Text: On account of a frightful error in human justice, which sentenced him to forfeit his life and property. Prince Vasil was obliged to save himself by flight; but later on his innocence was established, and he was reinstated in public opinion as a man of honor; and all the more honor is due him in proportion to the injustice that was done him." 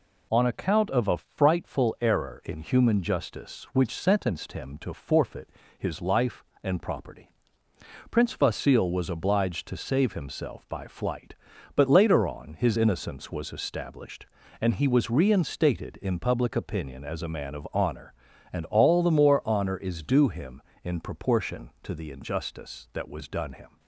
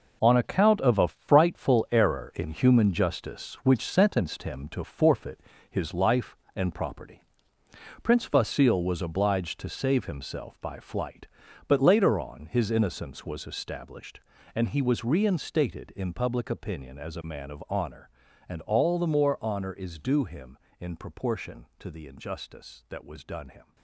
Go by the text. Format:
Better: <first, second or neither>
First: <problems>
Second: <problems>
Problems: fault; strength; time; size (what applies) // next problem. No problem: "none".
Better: first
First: pauses between "forfeit" and "his"; slight; at 5.4 s; 0.29 s long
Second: gets quieter; strong; throughout; 9.5 dB // pauses between "forfeit" and "his"; slight; at 5.3 s; 0.30 s long